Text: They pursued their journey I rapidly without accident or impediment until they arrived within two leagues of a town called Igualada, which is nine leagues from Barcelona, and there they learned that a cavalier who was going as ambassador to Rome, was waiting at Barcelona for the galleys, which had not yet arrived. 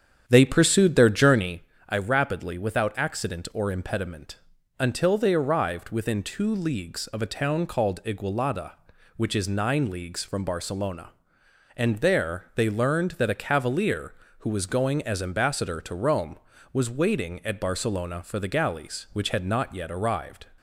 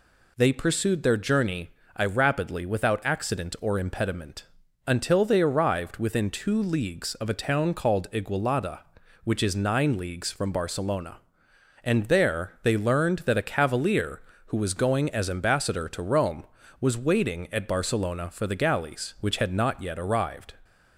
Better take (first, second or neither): second